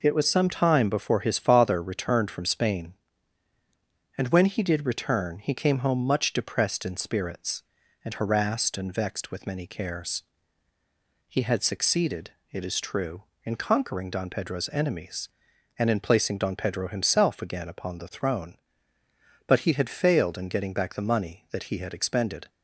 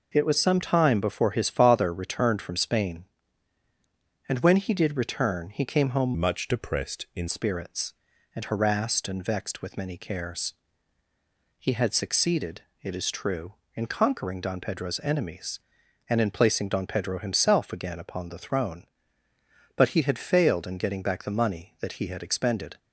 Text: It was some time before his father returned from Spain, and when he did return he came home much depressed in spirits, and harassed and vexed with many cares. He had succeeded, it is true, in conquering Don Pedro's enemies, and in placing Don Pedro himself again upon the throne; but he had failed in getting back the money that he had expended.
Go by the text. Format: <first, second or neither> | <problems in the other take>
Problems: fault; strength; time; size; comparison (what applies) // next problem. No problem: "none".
first | changes voice from "much" to "in"; from 6.1 to 7.2 s; 1.1 s long